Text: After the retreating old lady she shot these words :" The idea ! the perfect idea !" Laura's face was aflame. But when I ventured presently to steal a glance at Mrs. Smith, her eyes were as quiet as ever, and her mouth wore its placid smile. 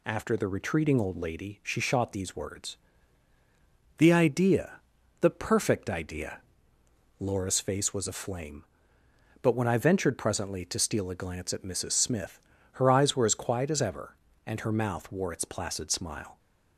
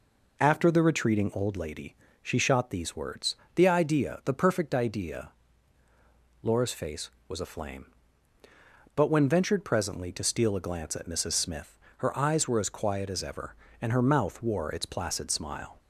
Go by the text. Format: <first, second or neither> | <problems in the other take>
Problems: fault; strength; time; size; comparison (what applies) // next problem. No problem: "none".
first | pauses between "lady" and "she"; slight; at 1.9 s; 0.26 s long // skips "I"; at 9.2 s